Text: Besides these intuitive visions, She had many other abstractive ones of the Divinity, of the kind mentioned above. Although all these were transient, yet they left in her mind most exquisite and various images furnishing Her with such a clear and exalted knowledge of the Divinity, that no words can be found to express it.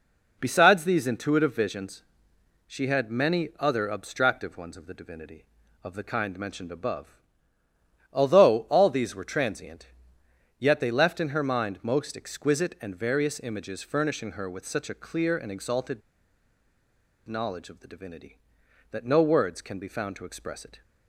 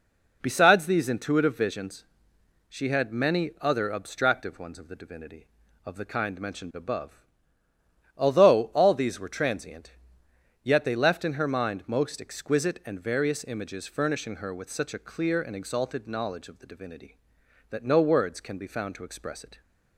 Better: second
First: pauses between "exalted" and "knowledge"; strong; at 16.0 s; 1.2 s long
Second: none

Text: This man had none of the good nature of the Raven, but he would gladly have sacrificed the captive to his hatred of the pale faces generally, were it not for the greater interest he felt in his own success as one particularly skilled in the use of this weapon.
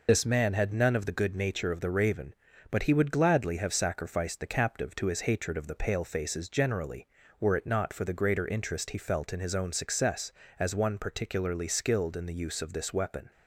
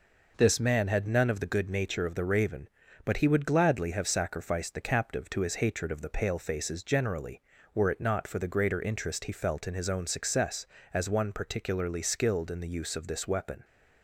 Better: second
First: loses the start of "This"; at 0.0 s; 65 ms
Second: none

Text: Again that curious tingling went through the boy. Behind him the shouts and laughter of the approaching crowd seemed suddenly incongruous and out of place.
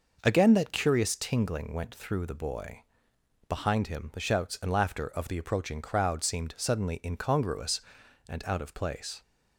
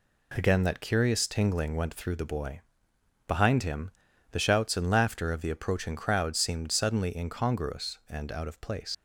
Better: first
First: none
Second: pauses between "him" and "the"; at 3.9 s; 0.40 s long // leaves "place" unfinished; at 8.9 s; 95 ms

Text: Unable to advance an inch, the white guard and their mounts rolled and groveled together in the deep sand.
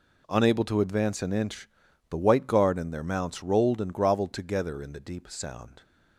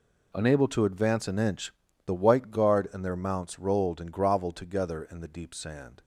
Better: second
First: says "sound" for "sand"; at 5.2 s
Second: none

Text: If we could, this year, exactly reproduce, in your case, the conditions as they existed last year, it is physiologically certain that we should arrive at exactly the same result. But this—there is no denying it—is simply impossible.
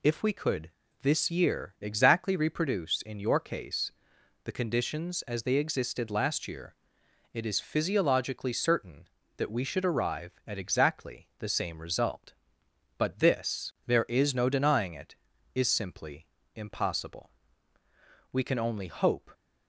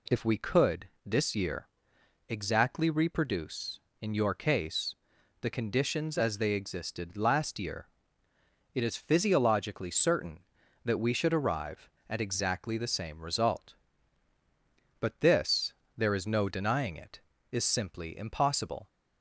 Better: second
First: pauses between "simply" and "impossible"; slight; at 16.2 s; 0.28 s long // goes on to say "We can only hope"; noticeable; from 18.3 s on; 0.98 s long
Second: none

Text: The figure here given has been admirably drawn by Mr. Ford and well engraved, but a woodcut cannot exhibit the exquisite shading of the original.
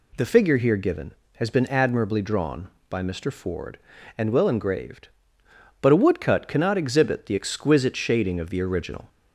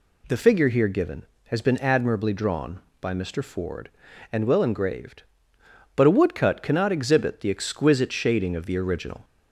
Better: neither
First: none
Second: none

